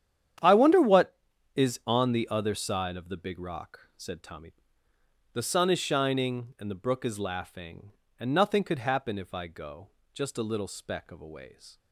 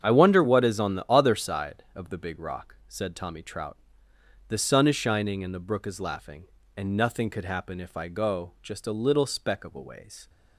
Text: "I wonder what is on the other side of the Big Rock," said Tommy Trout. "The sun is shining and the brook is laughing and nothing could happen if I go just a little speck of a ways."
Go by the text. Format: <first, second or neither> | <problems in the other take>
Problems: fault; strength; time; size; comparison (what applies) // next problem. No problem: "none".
second | starts louder than the rest; strong; until 1.7 s; 9.5 dB; strong in the second // skips "Trout"; at 4.9 s // pauses between "go" and "just"; slight; at 9.8 s; 0.24 s long